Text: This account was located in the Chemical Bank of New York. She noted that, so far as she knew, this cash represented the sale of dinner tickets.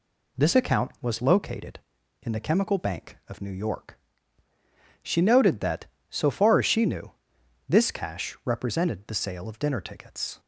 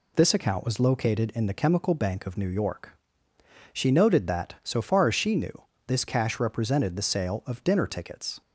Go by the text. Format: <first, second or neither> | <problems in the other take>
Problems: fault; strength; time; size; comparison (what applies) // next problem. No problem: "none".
neither | none